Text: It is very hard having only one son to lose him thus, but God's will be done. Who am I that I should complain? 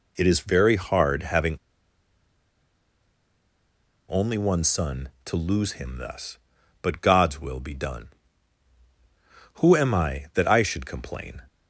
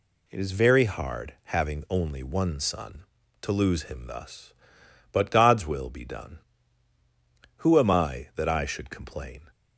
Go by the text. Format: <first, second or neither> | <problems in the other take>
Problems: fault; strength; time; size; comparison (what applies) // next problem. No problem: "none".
second | pauses between "having" and "only"; strong; at 1.5 s; 2.5 s long